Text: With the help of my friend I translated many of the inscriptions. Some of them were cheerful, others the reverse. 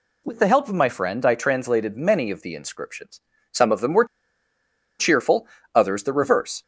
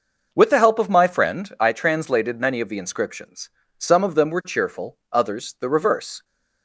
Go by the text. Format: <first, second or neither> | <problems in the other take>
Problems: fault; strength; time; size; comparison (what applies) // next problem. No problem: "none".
second | pauses between "were" and "cheerful"; noticeable; at 4.0 s; 0.94 s long